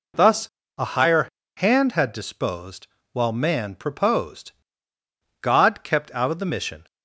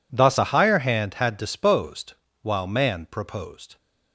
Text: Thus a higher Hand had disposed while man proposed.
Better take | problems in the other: second | pauses between "Thus" and "a"; slight; at 0.4 s; 0.30 s long // pauses between "higher" and "Hand"; slight; at 1.2 s; 0.32 s long // pauses between "disposed" and "while"; slight; at 2.8 s; 0.24 s long; slight in the second // goes on to say "God kept out of the mission"; from 5.4 s on; 1.4 s long

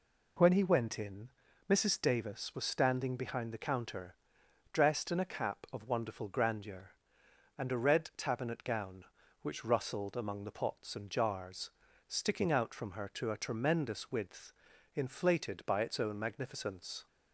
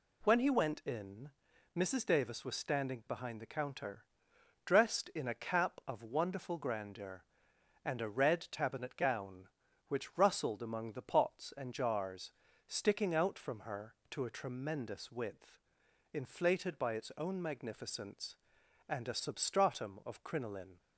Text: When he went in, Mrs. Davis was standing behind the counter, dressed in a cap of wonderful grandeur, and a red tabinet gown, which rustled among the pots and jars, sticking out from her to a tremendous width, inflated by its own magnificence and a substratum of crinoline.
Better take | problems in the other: second | stops before "and a substratum of crinoline"; at 17.0 s

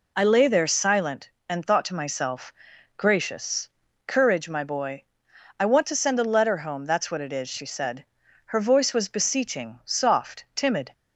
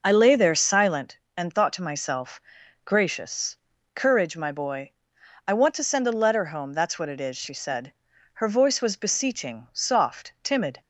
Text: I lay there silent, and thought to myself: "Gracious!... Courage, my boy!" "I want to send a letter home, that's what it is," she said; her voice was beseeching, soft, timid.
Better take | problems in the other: first | starts louder than the rest; noticeable; until 1.1 s; 5.5 dB

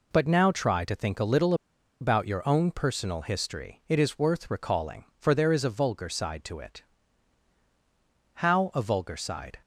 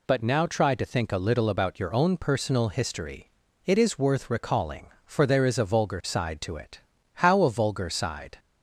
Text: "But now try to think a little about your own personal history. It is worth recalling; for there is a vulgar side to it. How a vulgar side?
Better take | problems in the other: second | pauses between "little" and "about"; noticeable; at 1.5 s; 0.47 s long

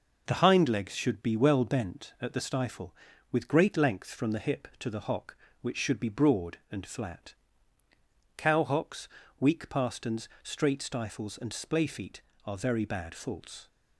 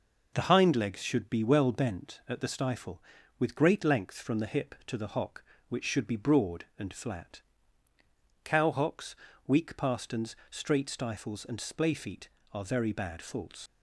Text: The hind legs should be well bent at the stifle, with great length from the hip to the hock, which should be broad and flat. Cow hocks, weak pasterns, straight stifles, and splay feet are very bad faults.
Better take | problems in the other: first | leaves "faults" unfinished; at 13.6 s; 90 ms

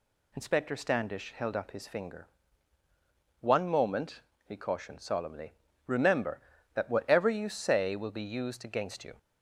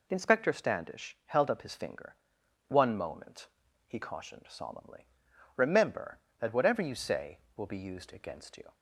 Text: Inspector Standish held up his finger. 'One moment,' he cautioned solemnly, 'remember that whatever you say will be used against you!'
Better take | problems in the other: neither | none

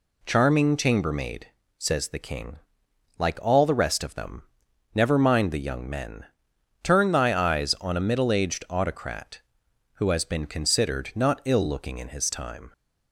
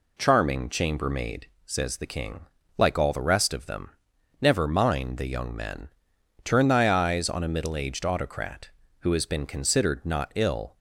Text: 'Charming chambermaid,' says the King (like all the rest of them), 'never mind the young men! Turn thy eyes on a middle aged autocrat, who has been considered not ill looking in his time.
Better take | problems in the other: first | stops before "looking in his time"; at 10.7 s

